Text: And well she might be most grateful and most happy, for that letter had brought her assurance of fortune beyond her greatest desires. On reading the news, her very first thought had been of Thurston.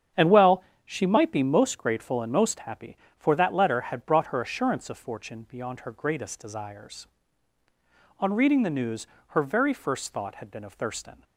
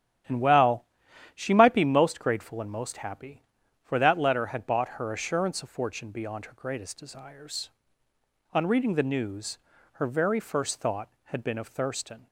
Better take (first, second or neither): first